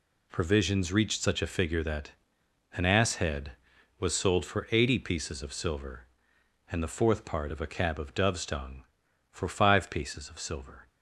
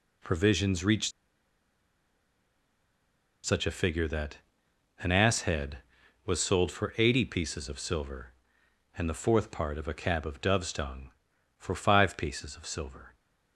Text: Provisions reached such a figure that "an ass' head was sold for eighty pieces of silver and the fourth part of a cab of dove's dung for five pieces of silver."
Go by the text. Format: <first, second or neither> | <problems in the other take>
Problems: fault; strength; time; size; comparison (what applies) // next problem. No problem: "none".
first | pauses between "reached" and "such"; strong; at 1.1 s; 2.3 s long // pauses between "that" and "an"; noticeable; at 4.3 s; 0.60 s long; noticeable in the first